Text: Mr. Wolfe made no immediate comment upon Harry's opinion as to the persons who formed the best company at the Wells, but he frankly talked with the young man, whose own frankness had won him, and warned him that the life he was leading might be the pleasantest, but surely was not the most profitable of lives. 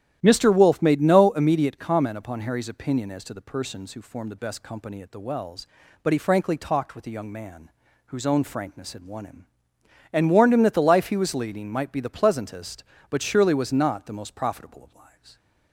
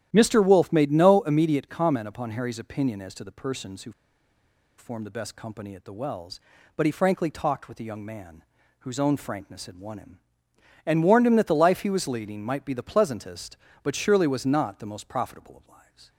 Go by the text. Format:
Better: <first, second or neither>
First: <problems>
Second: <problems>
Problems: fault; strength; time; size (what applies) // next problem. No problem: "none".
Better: first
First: starts louder than the rest; strong; until 1.2 s; 12 dB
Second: starts louder than the rest; strong; until 1.1 s; 12 dB // pauses between "who" and "formed"; noticeable; at 3.9 s; 0.87 s long